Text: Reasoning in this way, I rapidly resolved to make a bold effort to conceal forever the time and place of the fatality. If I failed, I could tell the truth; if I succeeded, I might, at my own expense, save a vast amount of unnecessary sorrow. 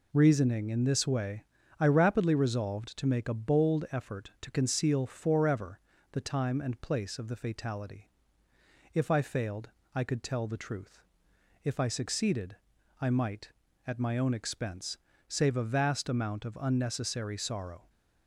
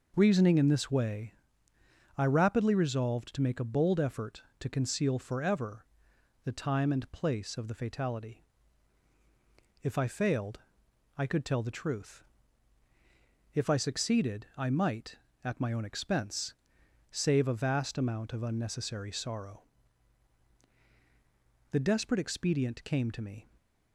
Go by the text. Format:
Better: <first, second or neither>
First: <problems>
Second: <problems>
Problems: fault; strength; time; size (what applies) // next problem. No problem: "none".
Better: first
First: pauses between "forever" and "the"; slight; at 5.7 s; 0.34 s long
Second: pauses between "forever" and "the"; noticeable; at 5.8 s; 0.60 s long // goes on to say "The desperate expedient came to me"; strong; from 21.7 s on; 1.7 s long